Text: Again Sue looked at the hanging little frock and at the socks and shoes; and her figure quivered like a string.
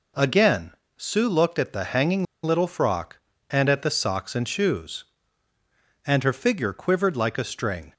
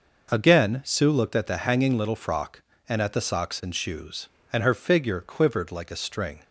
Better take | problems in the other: second | pauses between "Again" and "Sue"; slight; at 0.7 s; 0.26 s long // pauses between "hanging" and "little"; slight; at 2.2 s; 0.20 s long

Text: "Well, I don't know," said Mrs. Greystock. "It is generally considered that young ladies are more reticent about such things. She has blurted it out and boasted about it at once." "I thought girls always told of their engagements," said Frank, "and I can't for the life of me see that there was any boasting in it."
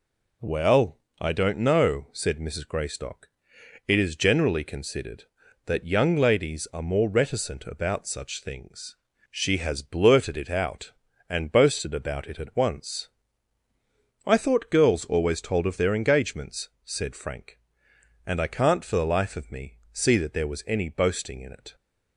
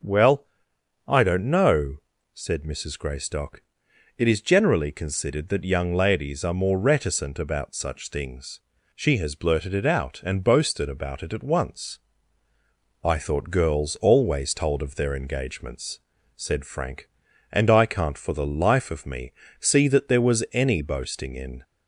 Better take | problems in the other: first | pauses between "me" and "see"; slight; at 19.3 s; 0.26 s long // stops before "it"; at 21.6 s

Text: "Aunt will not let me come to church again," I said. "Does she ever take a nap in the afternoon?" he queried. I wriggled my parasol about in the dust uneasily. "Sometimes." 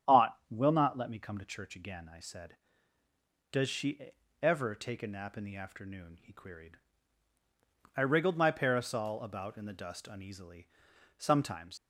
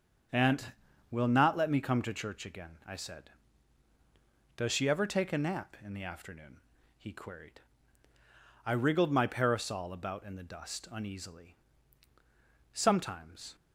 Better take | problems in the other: second | starts louder than the rest; strong; until 1.2 s; 9.5 dB; strong in the second // pauses between "she" and "ever"; slight; at 4.1 s; 0.28 s long // leaves "Sometimes" unfinished; at 11.7 s; 95 ms

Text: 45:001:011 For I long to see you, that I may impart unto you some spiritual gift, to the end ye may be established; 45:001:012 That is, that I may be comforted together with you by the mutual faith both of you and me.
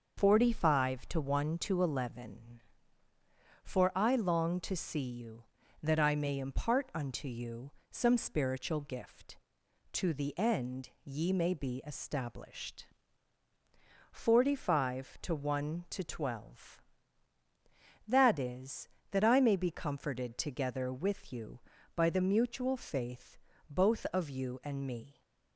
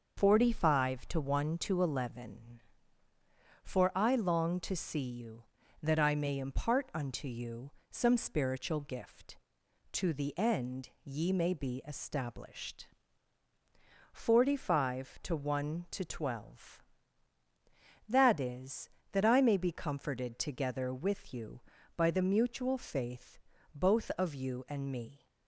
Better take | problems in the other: neither | pauses between "you" and "some"; slight; the same in both // pauses between "end" and "ye"; slight; the same in both // pauses between "faith" and "both"; slight; the same in both

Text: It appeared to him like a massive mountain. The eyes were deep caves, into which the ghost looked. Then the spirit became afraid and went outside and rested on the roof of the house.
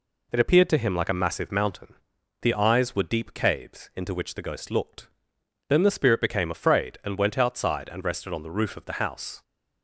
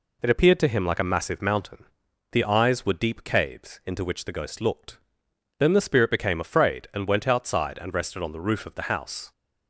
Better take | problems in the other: neither | none

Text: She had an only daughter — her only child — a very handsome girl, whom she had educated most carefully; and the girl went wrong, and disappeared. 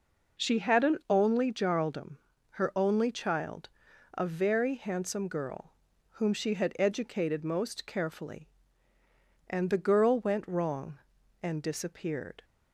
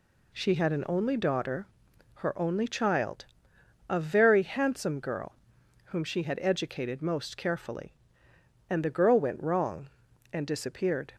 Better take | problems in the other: second | says "jarldom" for "daughter"; at 1.5 s

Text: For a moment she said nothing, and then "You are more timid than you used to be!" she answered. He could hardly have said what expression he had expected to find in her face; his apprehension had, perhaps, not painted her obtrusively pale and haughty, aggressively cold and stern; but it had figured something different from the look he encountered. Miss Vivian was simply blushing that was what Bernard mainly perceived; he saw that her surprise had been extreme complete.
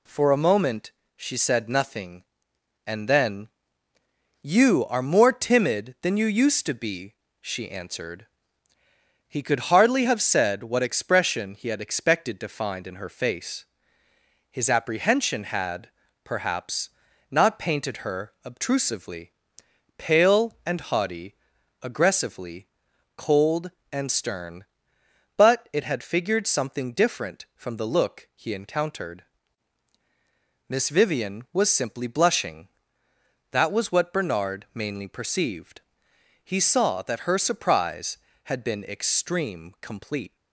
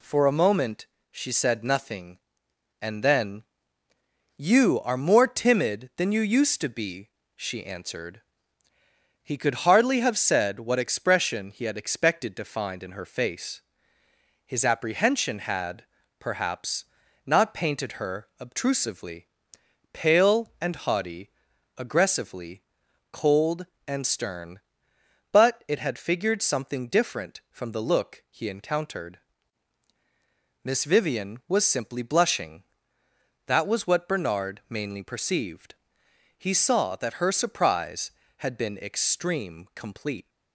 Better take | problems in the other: neither | pauses between "moment" and "she"; slight; the same in both // pauses between "then" and "You"; noticeable; the same in both // pauses between "obtrusively" and "pale"; noticeable; the same in both // pauses between "aggressively" and "cold"; noticeable; the same in both

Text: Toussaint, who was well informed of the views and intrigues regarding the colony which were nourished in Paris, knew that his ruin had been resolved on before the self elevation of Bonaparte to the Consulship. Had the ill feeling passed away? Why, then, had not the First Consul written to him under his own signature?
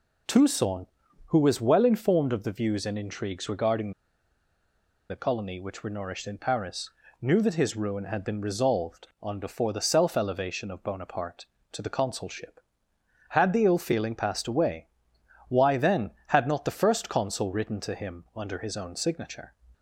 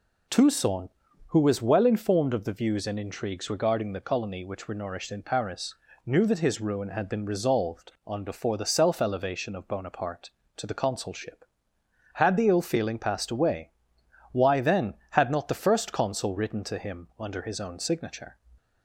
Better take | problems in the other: second | pauses between "regarding" and "the"; at 3.9 s; 1.1 s long

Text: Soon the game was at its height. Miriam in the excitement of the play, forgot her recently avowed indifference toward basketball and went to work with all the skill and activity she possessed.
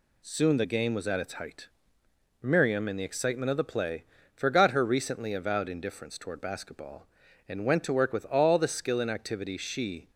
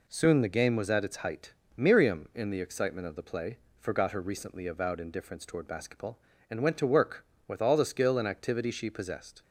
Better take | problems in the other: second | stops before "possessed"; at 10.0 s

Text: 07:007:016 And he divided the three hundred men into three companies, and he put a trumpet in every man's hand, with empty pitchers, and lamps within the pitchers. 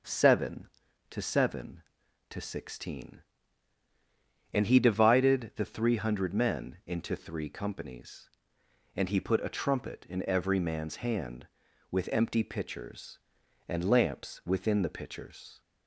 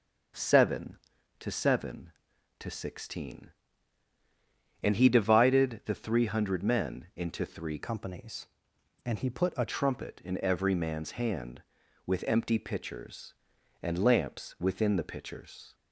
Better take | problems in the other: first | starts louder than the rest; until 1.7 s; 6.5 dB; also in the first // changes voice from "companies" to "a"; from 7.8 to 9.6 s; 1.8 s long

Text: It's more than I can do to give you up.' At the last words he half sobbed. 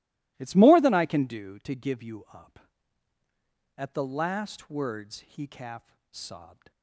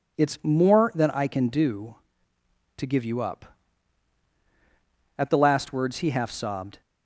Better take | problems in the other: second | says "calf" for "half"; at 5.4 s

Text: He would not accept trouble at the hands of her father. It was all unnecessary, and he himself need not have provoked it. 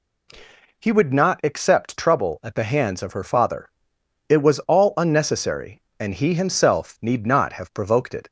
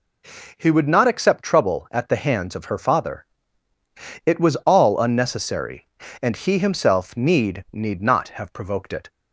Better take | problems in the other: first | says "need" twice; at 7.7 s

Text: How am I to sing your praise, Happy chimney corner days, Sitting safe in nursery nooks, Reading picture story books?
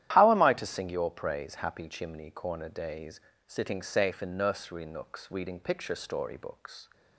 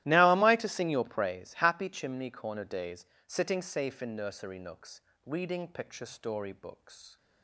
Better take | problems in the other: first | starts louder than the rest; strong; until 1.0 s; 15 dB; strong in the first // says "Now" for "How"; at 0.0 s

